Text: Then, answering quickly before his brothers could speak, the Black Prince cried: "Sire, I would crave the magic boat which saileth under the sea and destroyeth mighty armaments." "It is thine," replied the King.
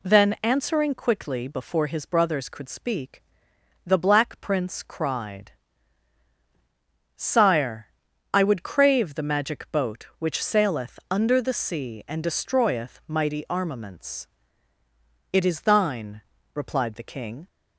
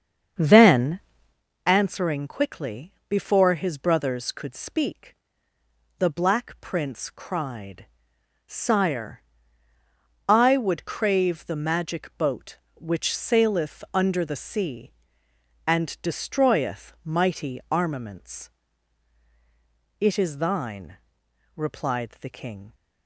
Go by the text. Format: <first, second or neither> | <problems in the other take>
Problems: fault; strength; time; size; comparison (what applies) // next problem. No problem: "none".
first | starts louder than the rest; strong; until 1.4 s; 7.5 dB // pauses between "quickly" and "before"; slight; at 2.9 s; 0.16 s long